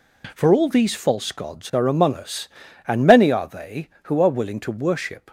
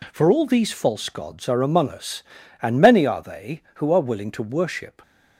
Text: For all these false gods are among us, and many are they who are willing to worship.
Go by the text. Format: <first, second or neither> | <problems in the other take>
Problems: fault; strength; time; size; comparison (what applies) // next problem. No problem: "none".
neither | none